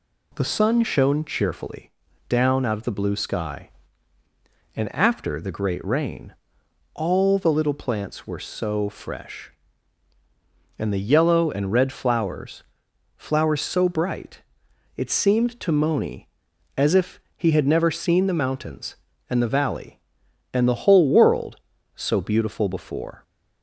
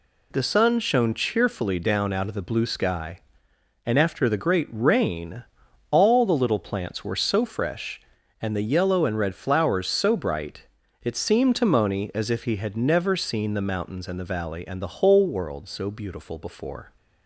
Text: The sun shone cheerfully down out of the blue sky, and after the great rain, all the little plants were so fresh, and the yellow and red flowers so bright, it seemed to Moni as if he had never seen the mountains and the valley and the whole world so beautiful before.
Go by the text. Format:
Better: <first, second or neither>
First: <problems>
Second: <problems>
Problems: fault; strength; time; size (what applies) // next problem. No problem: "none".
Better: second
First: pauses between "cheerfully" and "down"; slight; at 1.9 s; 0.36 s long // says "flowers" twice; at 13.1 s // pauses between "if" and "he"; slight; at 17.2 s; 0.16 s long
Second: none